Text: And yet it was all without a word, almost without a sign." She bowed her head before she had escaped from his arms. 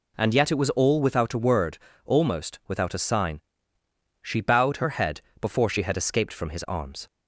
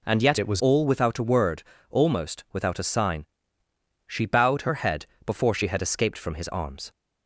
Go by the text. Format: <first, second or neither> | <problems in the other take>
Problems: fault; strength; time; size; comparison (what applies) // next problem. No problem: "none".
first | changes voice from "it" to "was"; from 0.3 to 0.6 s; 0.3 s long // pauses between "head" and "before"; slight; at 5.0 s; 0.18 s long; slight in the first